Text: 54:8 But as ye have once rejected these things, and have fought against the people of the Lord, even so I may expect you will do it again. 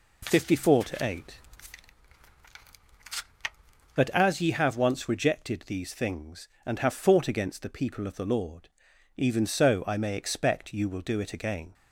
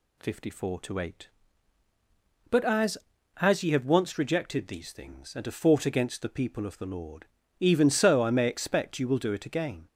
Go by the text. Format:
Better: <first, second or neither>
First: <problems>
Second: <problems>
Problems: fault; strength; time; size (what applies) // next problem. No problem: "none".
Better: first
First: none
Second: says "as" twice; at 3.4 s